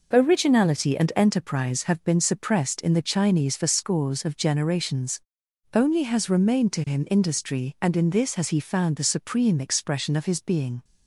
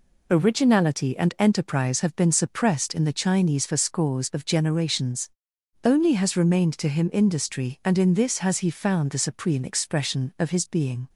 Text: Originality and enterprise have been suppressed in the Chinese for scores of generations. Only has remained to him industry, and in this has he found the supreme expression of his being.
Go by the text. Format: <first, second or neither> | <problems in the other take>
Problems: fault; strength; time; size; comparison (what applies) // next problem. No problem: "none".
neither | none